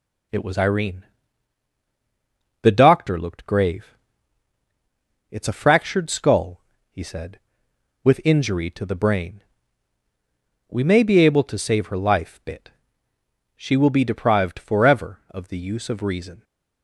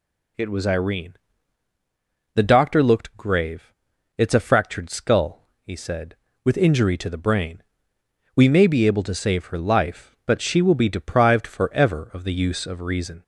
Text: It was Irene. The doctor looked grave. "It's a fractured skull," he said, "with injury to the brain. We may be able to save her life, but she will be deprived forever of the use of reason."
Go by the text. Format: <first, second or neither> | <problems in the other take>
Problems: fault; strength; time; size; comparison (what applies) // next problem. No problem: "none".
second | says "bit" for "but"; at 12.4 s